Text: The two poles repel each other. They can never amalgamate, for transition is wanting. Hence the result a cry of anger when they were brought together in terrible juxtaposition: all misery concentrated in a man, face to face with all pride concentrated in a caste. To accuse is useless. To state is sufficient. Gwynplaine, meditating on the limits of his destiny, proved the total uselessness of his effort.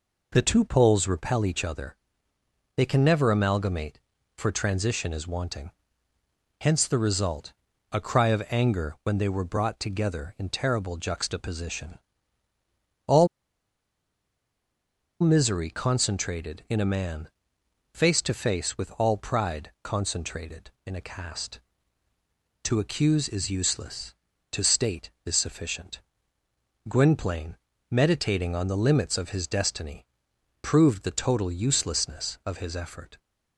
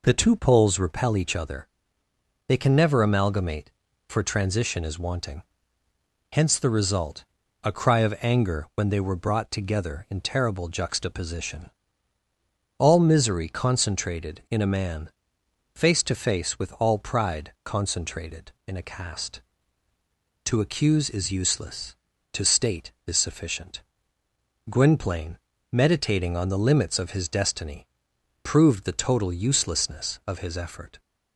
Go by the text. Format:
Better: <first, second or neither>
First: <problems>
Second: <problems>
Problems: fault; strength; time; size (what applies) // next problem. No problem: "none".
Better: second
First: pauses between "result" and "a"; at 7.5 s; 0.38 s long // pauses between "all" and "misery"; strong; at 13.2 s; 1.9 s long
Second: pauses between "result" and "a"; at 7.2 s; 0.38 s long